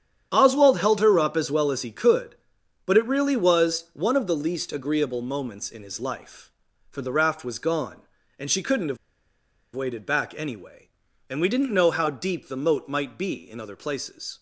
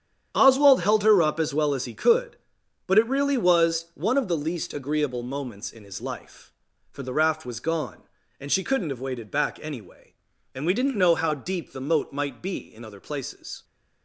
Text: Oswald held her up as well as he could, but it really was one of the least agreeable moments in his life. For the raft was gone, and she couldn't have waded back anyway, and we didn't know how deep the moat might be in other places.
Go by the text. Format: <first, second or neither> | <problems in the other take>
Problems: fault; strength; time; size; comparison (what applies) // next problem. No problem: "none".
second | starts louder than the rest; strong; until 1.3 s; 9 dB; strong in the second // pauses between "have" and "waded"; noticeable; at 8.9 s; 0.78 s long